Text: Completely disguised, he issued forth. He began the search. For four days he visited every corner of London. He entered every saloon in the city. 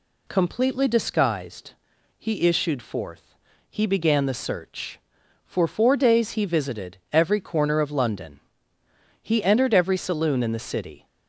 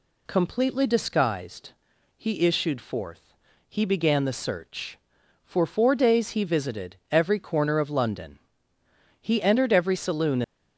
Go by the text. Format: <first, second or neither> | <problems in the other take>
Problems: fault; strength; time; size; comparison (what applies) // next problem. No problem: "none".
first | pauses between "visited" and "every"; slight; at 6.9 s; 0.16 s long; slight in the first // stops before "in the city"; at 10.4 s